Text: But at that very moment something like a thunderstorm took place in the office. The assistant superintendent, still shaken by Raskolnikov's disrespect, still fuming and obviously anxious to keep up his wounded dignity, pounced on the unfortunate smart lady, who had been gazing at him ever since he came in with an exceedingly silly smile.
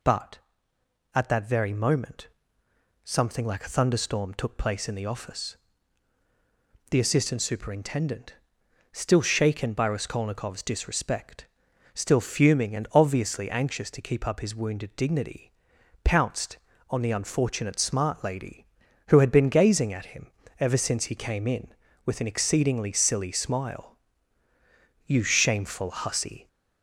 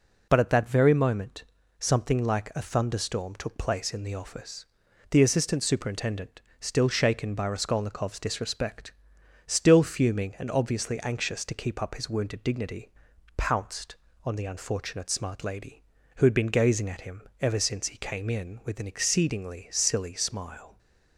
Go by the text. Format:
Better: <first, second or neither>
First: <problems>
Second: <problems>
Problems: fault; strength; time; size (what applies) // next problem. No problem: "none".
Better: second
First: pauses between "moment" and "something"; noticeable; at 2.2 s; 0.76 s long // pauses between "him" and "ever"; slight; at 20.2 s; 0.32 s long // goes on to say "You shameful hussy"; from 25.0 s on; 1.4 s long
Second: pauses between "moment" and "something"; slight; at 1.4 s; 0.36 s long // pauses between "him" and "ever"; slight; at 17.2 s; 0.18 s long